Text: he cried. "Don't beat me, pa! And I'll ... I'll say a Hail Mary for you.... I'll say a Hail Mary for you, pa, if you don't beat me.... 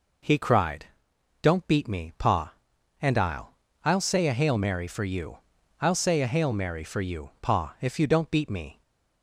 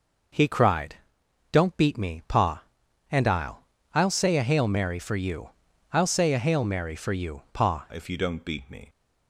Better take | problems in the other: first | changes voice at "if"; from 7.9 s on; 0.9 s long

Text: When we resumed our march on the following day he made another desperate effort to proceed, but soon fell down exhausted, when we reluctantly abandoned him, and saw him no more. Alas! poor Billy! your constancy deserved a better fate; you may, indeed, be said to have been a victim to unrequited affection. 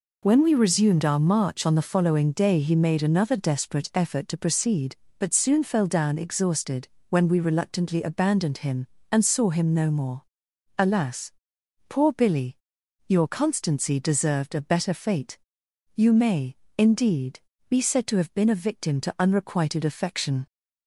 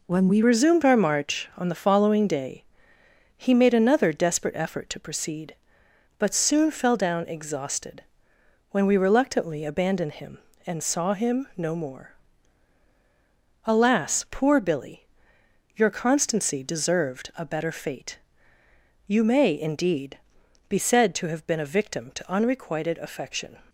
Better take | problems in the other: first | changes voice at "resumed"; from 0.4 s on; 23.1 s long // pauses between "day" and "he"; noticeable; at 2.6 s; 0.74 s long

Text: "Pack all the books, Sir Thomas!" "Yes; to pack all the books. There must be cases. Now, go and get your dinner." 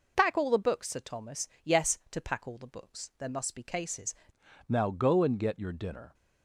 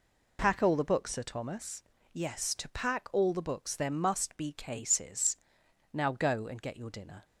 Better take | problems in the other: second | changes voice at "Now"; from 4.6 s on; 1.5 s long

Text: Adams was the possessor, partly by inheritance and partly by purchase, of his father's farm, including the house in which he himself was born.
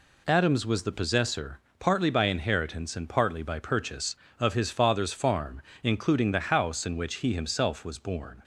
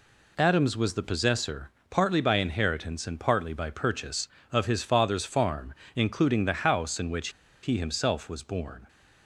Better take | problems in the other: first | pauses between "which" and "he"; slight; at 7.2 s; 0.33 s long

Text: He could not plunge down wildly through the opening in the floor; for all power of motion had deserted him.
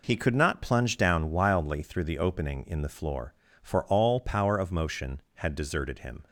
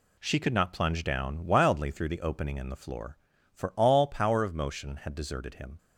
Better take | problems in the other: first | says "She" for "He"; at 0.1 s

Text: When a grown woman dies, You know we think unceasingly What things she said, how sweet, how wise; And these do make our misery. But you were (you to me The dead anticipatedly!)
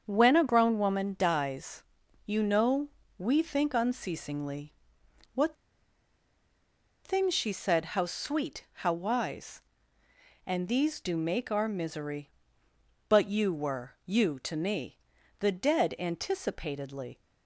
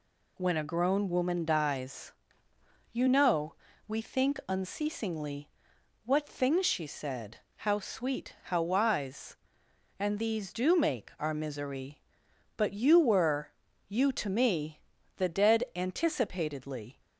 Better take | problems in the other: second | starts louder than the rest; strong; until 1.0 s; 7 dB // pauses between "know" and "we"; slight; at 2.8 s; 0.28 s long; slight in the second // pauses between "unceasingly" and "What"; noticeable; at 4.7 s; 0.58 s long; noticeable in the second // pauses between "What" and "things"; strong; at 5.5 s; 1.5 s long // pauses between "me" and "The"; at 14.9 s; 0.40 s long; also in the second

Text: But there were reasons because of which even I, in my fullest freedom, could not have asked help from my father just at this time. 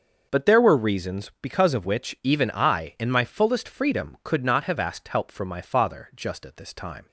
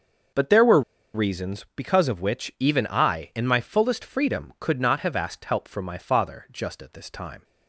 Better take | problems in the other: first | starts louder than the rest; noticeable; until 1.7 s; 6 dB; noticeable in the first // pauses between "were" and "reasons"; slight; at 0.8 s; 0.33 s long

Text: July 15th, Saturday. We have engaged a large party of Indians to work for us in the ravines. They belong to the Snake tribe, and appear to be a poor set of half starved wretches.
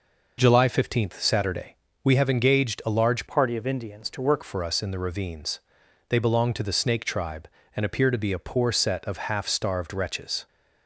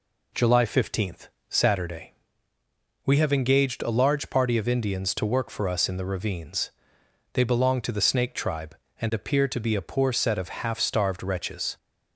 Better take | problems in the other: second | changes voice from "party" to "work"; from 3.2 to 4.4 s; 1.2 s long

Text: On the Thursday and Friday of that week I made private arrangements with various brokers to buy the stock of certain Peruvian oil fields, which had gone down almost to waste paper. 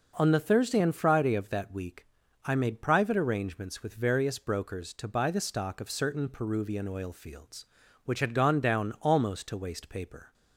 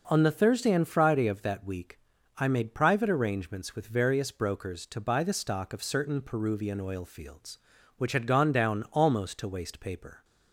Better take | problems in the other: neither | pauses between "week" and "I"; the same in both

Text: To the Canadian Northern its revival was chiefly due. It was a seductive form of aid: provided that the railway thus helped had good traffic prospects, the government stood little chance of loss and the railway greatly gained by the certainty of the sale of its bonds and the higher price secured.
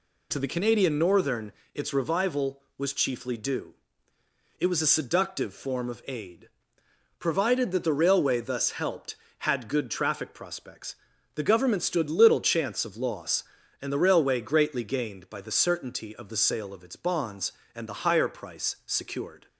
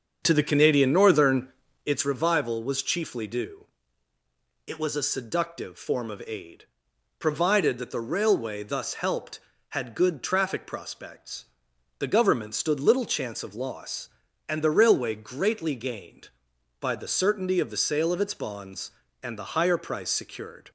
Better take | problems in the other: first | starts louder than the rest; until 2.0 s; 6.5 dB // pauses between "Northern" and "its"; slight; at 1.4 s; 0.36 s long; slight in the first

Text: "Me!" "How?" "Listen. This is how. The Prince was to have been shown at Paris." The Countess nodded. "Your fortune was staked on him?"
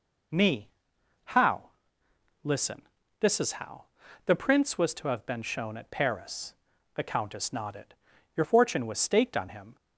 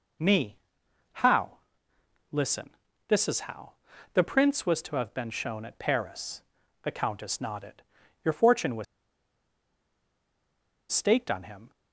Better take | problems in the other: first | pauses between "was" and "staked"; strong; at 8.8 s; 2.0 s long

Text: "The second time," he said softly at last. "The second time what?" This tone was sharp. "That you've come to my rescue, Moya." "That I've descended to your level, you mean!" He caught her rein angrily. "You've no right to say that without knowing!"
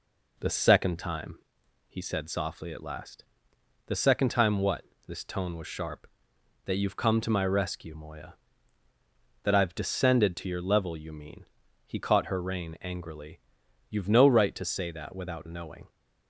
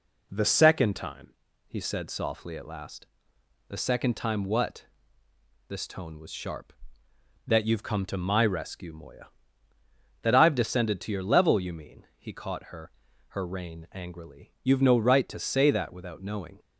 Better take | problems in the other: first | says "her" twice; at 13.2 s

